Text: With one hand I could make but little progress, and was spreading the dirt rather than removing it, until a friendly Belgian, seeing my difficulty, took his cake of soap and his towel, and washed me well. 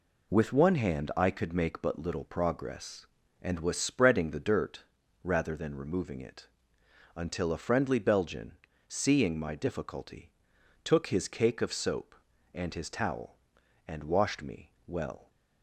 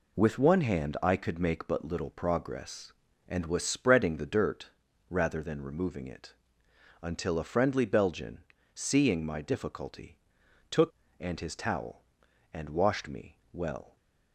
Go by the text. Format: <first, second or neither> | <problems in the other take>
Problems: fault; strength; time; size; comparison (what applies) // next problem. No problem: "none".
first | pauses between "dirt" and "rather"; at 4.7 s; 0.40 s long; also in the first // skips "his cake of soap"; at 11.0 s